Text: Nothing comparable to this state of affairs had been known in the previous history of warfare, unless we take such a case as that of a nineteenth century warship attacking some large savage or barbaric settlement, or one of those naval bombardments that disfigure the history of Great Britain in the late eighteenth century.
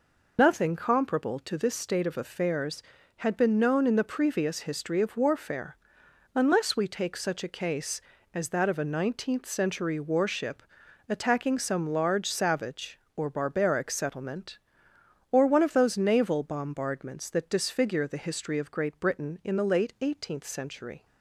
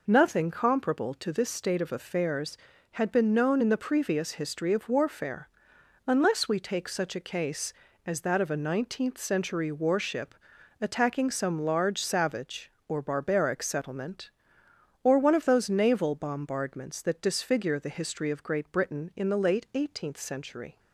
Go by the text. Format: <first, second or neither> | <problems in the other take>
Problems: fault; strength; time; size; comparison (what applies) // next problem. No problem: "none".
second | loses the start of "Nothing"; at 0.3 s; 65 ms // pauses between "warship" and "attacking"; noticeable; at 10.6 s; 0.46 s long; noticeable in the second